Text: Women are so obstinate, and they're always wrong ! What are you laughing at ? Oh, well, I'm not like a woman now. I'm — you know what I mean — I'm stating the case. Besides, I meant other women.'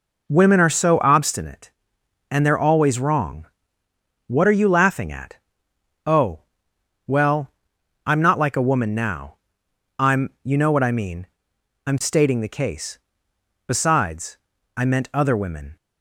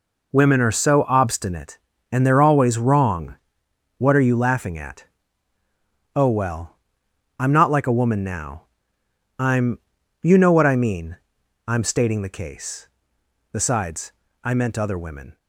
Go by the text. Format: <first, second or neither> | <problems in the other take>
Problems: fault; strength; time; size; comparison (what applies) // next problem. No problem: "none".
neither | none